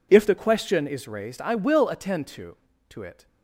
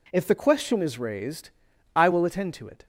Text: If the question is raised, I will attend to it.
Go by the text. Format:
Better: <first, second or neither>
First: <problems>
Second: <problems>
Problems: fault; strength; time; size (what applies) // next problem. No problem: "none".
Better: second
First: says "to" twice; at 2.9 s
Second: none